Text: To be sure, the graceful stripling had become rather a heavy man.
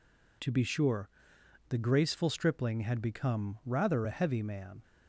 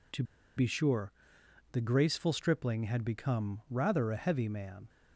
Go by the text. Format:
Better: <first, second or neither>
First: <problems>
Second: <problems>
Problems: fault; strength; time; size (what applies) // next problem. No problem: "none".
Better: first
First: none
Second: pauses between "To" and "be"; slight; at 0.2 s; 0.33 s long